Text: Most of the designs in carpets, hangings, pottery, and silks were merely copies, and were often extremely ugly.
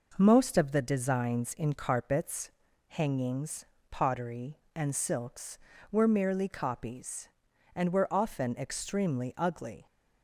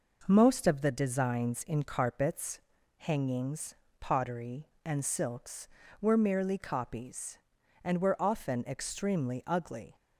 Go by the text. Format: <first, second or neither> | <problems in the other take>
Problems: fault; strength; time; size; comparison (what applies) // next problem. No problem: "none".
neither | none